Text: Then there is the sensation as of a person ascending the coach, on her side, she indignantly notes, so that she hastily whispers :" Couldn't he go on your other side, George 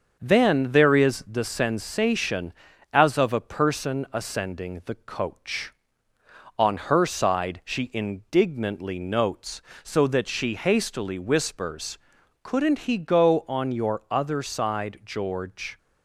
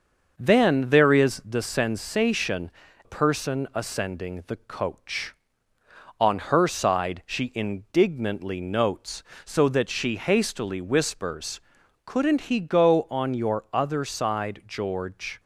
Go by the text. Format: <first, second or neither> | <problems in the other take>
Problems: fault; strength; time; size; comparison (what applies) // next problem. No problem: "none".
first | starts louder than the rest; until 1.3 s; 6 dB; also in the first // skips "as of a"; at 2.8 s